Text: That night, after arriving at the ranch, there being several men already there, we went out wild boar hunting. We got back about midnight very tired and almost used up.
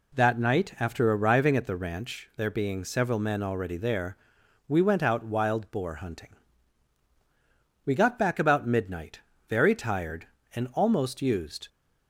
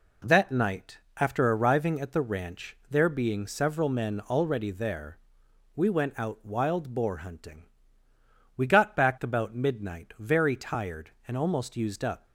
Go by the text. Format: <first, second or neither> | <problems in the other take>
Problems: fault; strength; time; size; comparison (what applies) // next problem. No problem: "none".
second | pauses between "midnight" and "very"; slight; at 9.1 s; 0.28 s long // stops before "up"; at 11.6 s